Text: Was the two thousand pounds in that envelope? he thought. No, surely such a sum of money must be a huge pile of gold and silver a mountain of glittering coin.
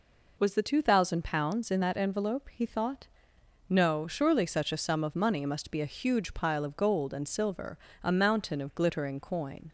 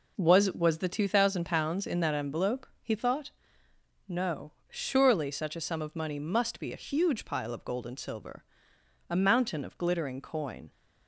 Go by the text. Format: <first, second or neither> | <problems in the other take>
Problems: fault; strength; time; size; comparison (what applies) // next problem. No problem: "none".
first | says "Was" twice; at 0.5 s // pauses between "silver" and "a"; noticeable; at 8.4 s; 0.66 s long; slight in the first